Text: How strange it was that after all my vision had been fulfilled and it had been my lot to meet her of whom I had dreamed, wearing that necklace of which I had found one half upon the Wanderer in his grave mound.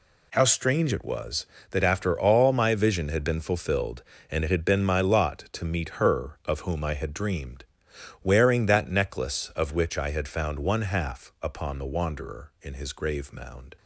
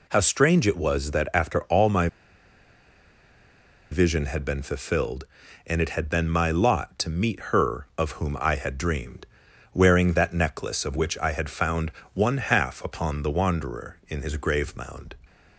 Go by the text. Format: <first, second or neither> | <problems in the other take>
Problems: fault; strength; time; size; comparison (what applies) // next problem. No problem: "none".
first | pauses between "my" and "vision"; strong; at 2.0 s; 1.8 s long // pauses between "found" and "one"; slight; at 11.9 s; 0.22 s long